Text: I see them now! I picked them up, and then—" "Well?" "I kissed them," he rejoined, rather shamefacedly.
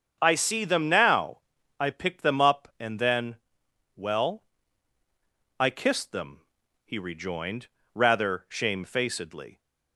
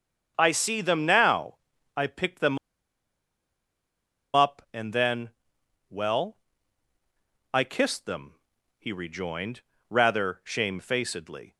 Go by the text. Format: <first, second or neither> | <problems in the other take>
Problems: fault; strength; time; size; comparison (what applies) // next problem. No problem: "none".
first | starts louder than the rest; strong; until 1.3 s; 7 dB; strong in the first // pauses between "them" and "up"; strong; at 2.5 s; 1.7 s long